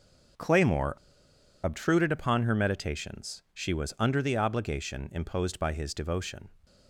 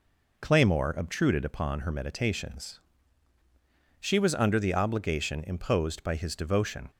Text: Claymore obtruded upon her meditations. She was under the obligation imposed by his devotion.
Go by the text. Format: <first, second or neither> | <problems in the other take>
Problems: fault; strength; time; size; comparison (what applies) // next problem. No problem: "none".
second | starts louder than the rest; until 2.0 s; 6.5 dB // pauses between "Claymore" and "obtruded"; noticeable; at 0.9 s; 0.68 s long